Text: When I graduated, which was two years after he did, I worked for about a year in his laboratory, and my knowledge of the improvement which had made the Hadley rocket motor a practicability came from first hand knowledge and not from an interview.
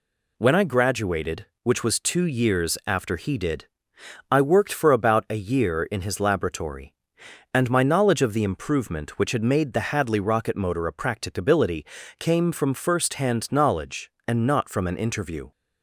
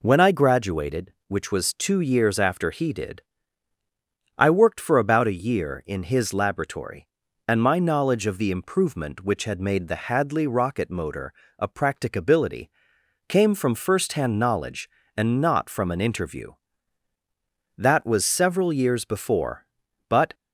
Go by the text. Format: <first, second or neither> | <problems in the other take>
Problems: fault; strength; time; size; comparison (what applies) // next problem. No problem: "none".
first | pauses between "motor" and "a"; slight; at 11.3 s; 0.28 s long // pauses between "practicability" and "came"; noticeable; at 12.6 s; 0.60 s long; slight in the first // goes on to say "That was several years before but"; strong; from 17.7 s on; 2.5 s long